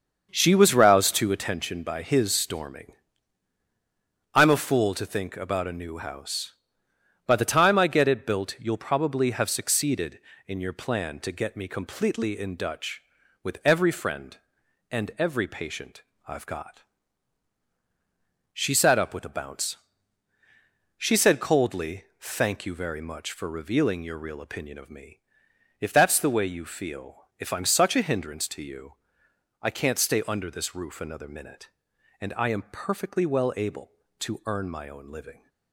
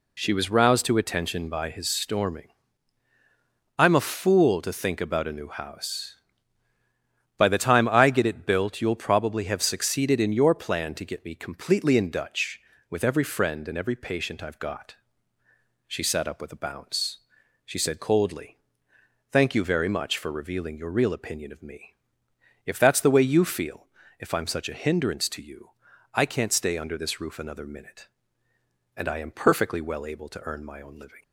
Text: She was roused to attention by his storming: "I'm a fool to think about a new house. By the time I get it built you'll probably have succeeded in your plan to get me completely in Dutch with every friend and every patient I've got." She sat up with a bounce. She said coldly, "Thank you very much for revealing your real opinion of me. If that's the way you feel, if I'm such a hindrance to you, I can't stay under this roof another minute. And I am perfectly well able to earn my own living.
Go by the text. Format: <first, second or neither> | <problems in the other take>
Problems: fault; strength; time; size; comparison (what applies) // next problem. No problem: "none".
second | starts louder than the rest; until 1.6 s; 6.5 dB // pauses between "patient" and "I've"; slight; at 16.0 s; 0.24 s long